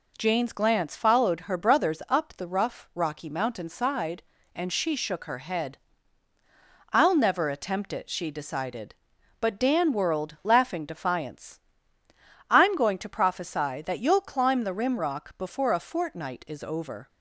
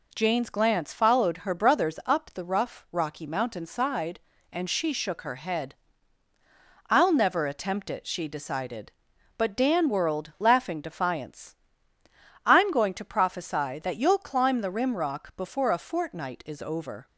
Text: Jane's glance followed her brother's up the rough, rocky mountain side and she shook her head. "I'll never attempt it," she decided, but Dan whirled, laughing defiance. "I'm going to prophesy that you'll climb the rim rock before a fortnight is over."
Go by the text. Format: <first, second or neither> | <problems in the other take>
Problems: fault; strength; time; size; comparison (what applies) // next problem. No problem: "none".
neither | none